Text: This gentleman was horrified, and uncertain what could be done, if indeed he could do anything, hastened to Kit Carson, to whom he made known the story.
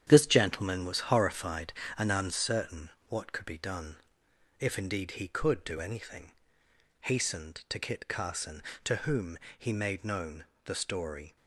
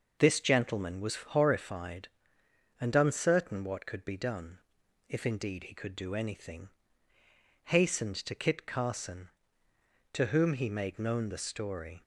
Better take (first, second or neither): second